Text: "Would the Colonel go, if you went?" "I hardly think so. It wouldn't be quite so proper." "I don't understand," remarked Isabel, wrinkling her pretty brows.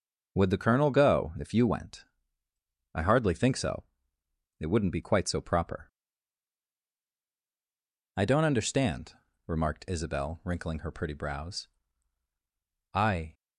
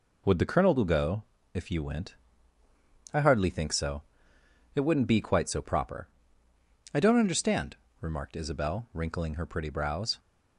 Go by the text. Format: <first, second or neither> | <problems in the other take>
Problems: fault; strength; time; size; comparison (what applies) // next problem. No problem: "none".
second | goes on to say "I"; slight; from 12.9 s on; 0.40 s long